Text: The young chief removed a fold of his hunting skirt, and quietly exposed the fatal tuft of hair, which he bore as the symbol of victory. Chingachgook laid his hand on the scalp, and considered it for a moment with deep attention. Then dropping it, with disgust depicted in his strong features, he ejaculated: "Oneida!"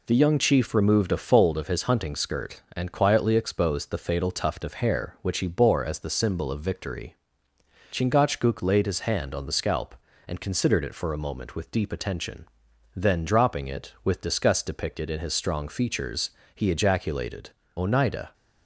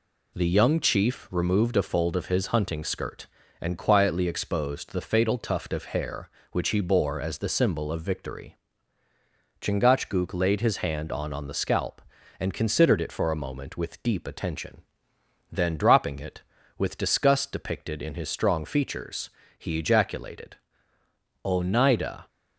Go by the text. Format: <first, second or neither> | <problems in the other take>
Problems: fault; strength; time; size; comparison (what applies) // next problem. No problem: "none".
first | says "on" twice; at 11.3 s